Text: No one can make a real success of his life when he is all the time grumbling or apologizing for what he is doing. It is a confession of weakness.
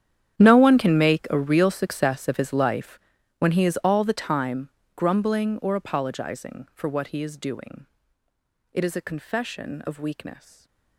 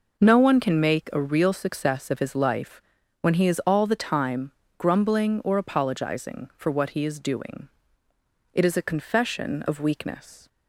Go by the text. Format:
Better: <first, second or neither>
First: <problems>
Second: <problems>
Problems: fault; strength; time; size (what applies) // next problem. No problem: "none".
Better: second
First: gets quieter; strong; throughout; 18.5 dB // pauses between "life" and "when"; at 2.9 s; 0.40 s long // pauses between "time" and "grumbling"; slight; at 4.6 s; 0.28 s long // stays silent after the last word; slight; from 10.3 s on; 0.6 s long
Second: pauses between "life" and "when"; at 2.8 s; 0.40 s long // pauses between "time" and "grumbling"; slight; at 4.5 s; 0.28 s long